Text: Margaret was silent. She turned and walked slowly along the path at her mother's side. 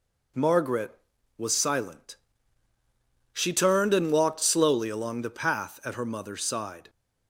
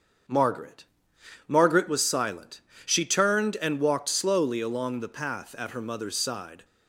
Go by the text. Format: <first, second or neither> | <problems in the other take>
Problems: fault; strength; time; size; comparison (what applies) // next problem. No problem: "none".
first | starts louder than the rest; strong; until 1.9 s; 7.5 dB // says "Margaret" twice; at 1.4 s